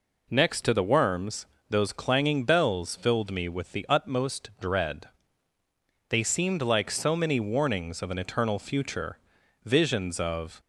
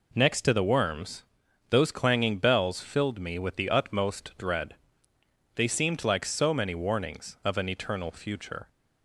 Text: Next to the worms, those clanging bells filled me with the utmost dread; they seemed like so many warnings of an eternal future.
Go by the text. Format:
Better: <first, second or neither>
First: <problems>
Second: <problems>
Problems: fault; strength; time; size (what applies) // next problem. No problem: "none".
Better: second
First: goes on to say "Visions of"; noticeable; from 9.6 s on; 0.96 s long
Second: none